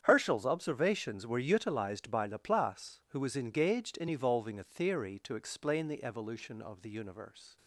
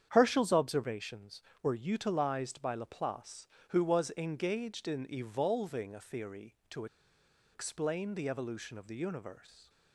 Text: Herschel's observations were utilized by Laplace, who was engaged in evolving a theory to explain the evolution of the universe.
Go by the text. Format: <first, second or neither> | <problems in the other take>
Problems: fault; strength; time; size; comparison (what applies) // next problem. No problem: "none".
first | starts louder than the rest; strong; until 1.1 s; 8.5 dB; strong in the first // pauses between "to" and "explain"; noticeable; at 6.8 s; 0.68 s long